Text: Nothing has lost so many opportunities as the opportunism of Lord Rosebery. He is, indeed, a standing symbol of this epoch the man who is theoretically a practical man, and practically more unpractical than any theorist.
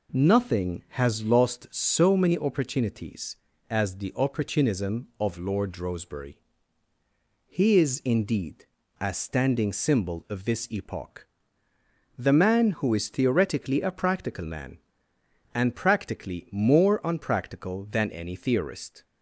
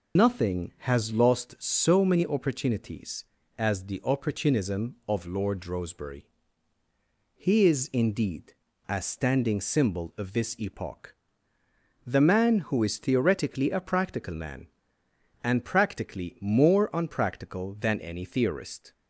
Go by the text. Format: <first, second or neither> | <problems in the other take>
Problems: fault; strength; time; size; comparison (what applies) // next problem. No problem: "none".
first | loses the start of "Nothing"; at 0.1 s; 165 ms // pauses between "epoch" and "the"; noticeable; at 11.1 s; 0.92 s long; noticeable in the first